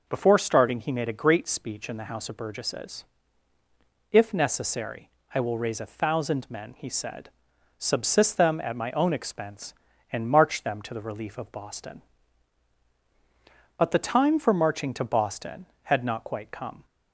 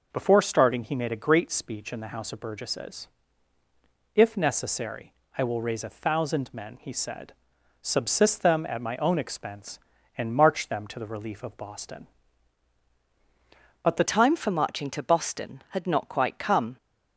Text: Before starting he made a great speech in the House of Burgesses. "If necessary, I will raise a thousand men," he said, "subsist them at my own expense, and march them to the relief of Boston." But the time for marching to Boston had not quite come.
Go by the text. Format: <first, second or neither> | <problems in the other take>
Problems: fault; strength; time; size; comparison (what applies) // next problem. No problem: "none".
first | changes voice at "time"; from 14.0 s on; 2.7 s long